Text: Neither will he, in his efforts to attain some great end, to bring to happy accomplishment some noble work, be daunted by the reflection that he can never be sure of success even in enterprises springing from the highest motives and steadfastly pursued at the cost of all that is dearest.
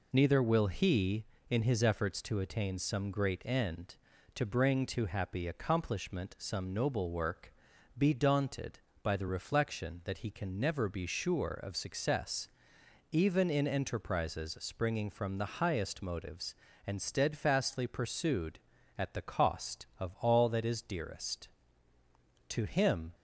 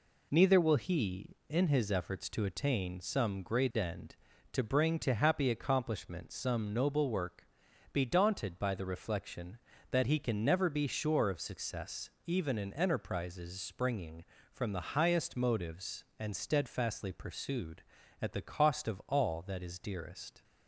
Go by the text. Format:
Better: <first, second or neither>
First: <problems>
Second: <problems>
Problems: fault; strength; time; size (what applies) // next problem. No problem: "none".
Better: second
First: pauses between "success" and "even"; noticeable; at 12.4 s; 0.64 s long // goes on to say "To him"; noticeable; from 22.4 s on; 0.64 s long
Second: pauses between "success" and "even"; slight; at 12.1 s; 0.16 s long